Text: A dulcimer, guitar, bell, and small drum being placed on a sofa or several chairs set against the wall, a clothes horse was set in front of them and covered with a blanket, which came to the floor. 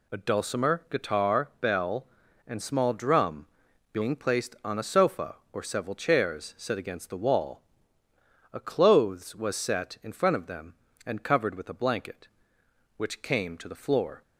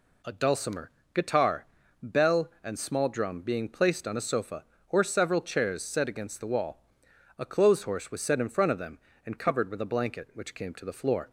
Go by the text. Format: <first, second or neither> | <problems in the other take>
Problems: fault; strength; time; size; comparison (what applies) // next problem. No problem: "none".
second | pauses between "drum" and "being"; noticeable; at 3.4 s; 0.46 s long // skips "horse"; at 9.3 s